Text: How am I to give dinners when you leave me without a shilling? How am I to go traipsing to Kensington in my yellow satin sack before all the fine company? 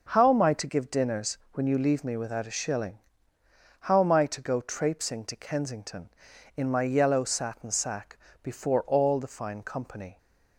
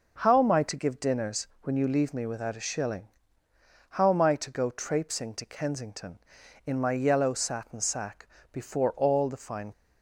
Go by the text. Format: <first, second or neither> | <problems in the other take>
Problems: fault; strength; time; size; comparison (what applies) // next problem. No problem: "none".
first | pauses between "sack" and "before"; slight; at 8.2 s; 0.26 s long; slight in the first // stops before "company"; at 9.7 s